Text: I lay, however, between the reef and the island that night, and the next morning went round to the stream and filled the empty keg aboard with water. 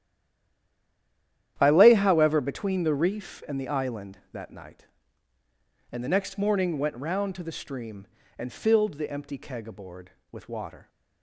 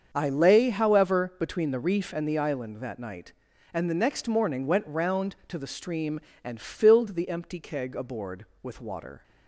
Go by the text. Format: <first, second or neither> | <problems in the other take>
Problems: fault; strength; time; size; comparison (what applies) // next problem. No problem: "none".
second | stays silent before the first word; noticeable; until 1.5 s; 1.5 s long // starts louder than the rest; strong; until 2.5 s; 10.5 dB; also in the second